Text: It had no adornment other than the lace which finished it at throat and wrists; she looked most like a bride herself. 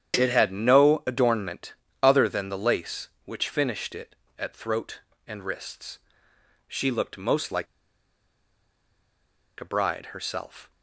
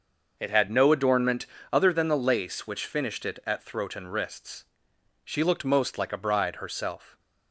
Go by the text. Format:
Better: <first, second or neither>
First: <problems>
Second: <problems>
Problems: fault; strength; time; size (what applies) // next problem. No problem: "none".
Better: second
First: starts louder than the rest; strong; until 1.1 s; 9 dB // pauses between "adornment" and "other"; slight; at 1.7 s; 0.28 s long // pauses between "like" and "a"; strong; at 7.6 s; 1.9 s long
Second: starts louder than the rest; noticeable; until 1.4 s; 6 dB // pauses between "adornment" and "other"; slight; at 1.4 s; 0.24 s long